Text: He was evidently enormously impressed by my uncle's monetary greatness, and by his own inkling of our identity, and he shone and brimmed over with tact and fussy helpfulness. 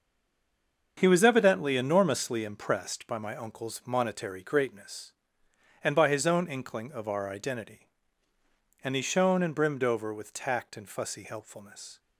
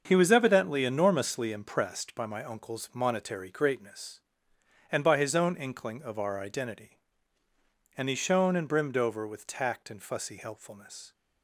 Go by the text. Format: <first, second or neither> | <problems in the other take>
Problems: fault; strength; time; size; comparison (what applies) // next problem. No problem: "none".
second | stays silent before the first word; slight; until 0.9 s; 0.9 s long // starts louder than the rest; until 2.0 s; 7 dB; also in the second